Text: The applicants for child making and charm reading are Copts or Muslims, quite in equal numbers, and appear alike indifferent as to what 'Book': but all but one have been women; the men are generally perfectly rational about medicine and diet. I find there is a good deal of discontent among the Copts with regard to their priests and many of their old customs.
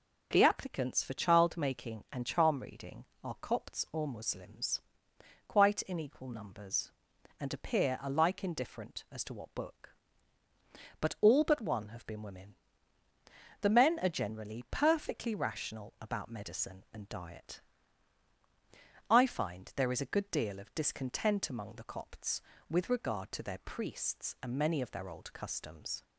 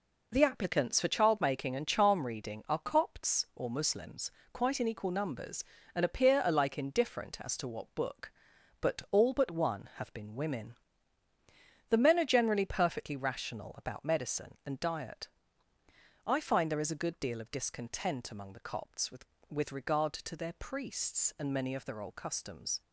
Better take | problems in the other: first | says "with" twice; at 19.5 s

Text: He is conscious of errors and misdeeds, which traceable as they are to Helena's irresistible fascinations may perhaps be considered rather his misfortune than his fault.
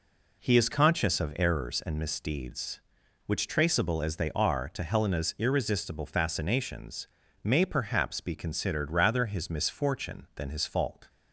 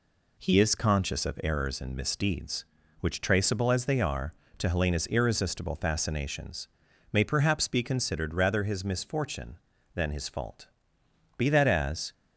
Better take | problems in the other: first | pauses between "fascinations" and "may"; at 6.6 s; 0.44 s long; slight in the first // goes on to say "Be that as"; noticeable; from 11.3 s on; 0.74 s long

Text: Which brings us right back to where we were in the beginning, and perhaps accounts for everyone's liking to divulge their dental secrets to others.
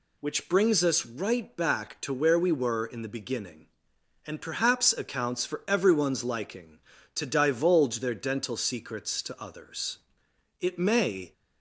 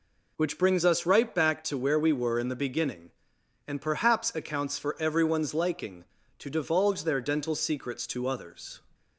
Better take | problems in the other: second | goes on to say "It may"; noticeable; from 10.6 s on; 0.72 s long

